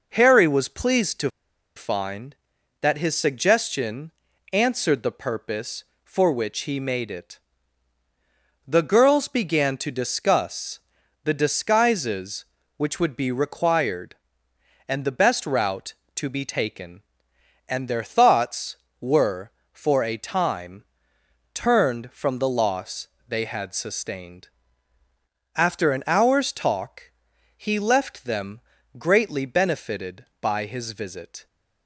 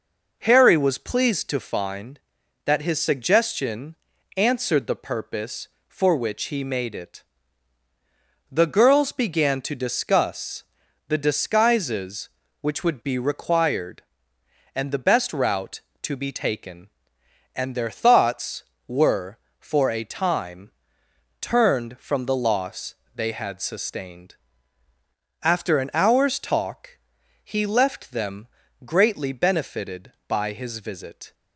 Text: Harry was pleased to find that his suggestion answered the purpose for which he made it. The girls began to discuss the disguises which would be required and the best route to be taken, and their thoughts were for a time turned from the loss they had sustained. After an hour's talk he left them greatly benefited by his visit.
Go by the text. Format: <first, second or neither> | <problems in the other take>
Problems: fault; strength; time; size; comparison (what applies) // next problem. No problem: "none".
second | pauses between "to" and "find"; noticeable; at 1.3 s; 0.46 s long // pauses between "suggestion" and "answered"; at 4.1 s; 0.42 s long; also in the second // pauses between "discuss" and "the"; noticeable; at 10.7 s; 0.46 s long; noticeable in the second // pauses between "time" and "turned"; noticeable; at 20.8 s; 0.70 s long; noticeable in the second // pauses between "loss" and "they"; slight; at 23.0 s; 0.22 s long; slight in the second // pauses between "talk" and "he"; noticeable; at 27.1 s; 0.46 s long; noticeable in the second // pauses between "them" and "greatly"; at 28.6 s; 0.38 s long; also in the second